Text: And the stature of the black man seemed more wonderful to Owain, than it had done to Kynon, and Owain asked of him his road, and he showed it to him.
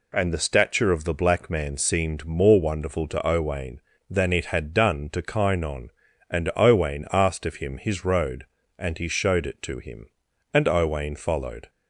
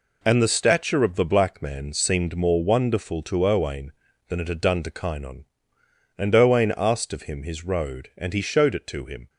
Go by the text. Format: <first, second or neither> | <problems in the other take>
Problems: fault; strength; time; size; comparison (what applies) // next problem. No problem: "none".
second | goes on to say "And Owain followed"; noticeable; from 10.5 s on; 1.1 s long